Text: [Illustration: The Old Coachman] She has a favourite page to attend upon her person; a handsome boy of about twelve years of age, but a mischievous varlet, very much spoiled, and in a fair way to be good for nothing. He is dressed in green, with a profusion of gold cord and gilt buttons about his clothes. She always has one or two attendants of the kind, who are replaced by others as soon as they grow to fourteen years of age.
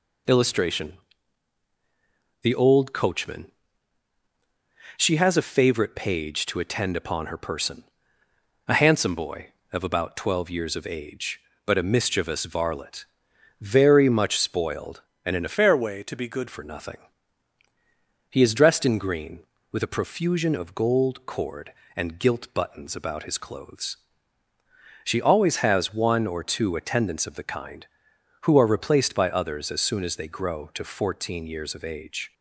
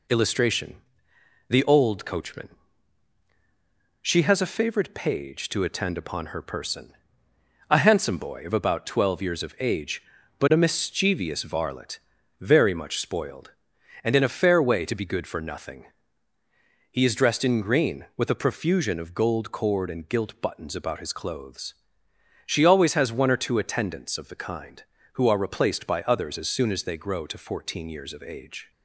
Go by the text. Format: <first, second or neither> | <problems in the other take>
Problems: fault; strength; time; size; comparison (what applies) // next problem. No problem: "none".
second | pauses between "Coachman" and "She"; strong; at 3.5 s; 1.4 s long; strong in the second // changes voice from "fair" to "good"; from 15.5 to 16.4 s; 0.9 s long